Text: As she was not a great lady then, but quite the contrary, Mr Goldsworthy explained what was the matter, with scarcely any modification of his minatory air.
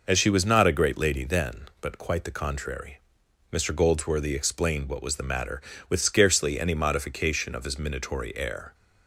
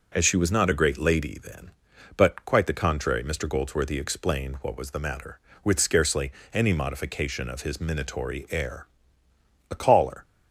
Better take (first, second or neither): first